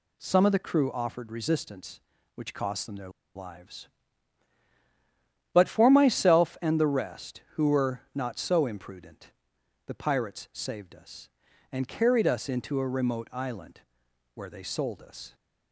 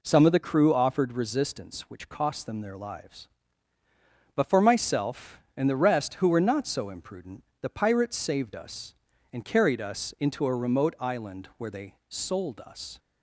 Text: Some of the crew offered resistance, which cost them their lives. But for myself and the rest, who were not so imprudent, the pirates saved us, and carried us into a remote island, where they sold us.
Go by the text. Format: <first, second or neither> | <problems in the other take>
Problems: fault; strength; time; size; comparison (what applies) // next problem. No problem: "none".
second | pauses between "their" and "lives"; slight; at 3.0 s; 0.26 s long